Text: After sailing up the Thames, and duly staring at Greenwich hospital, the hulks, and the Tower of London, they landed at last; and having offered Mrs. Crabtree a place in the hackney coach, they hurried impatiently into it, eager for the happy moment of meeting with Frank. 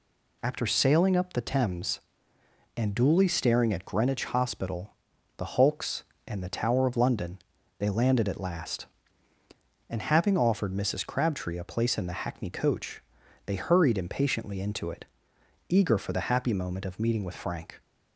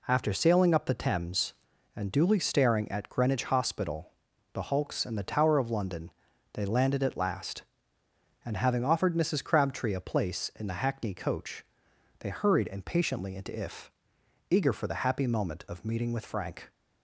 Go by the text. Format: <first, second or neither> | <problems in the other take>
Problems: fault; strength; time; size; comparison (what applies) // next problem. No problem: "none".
first | says "if" for "it"; at 13.5 s